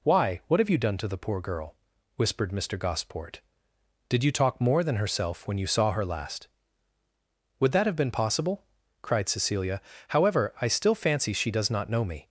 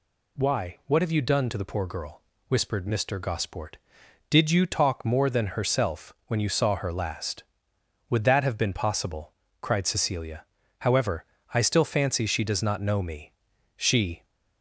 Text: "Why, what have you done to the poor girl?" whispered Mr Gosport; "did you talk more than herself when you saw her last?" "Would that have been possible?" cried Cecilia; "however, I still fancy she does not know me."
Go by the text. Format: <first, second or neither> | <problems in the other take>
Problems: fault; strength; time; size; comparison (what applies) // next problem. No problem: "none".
first | goes on to say "She"; slight; from 13.7 s on; 0.46 s long